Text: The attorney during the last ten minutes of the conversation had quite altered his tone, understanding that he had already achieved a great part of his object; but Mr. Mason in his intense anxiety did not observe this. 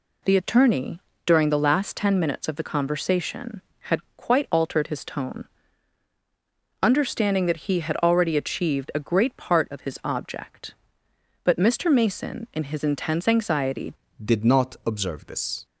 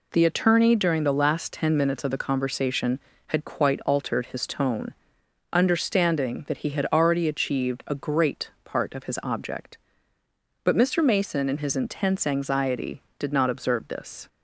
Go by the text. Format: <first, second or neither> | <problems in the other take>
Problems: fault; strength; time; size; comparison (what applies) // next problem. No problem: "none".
second | pauses between "attorney" and "during"; slight; at 0.9 s; 0.26 s long // pauses between "had" and "quite"; slight; at 3.9 s; 0.16 s long // changes voice at "did"; from 14.2 s on; 1.4 s long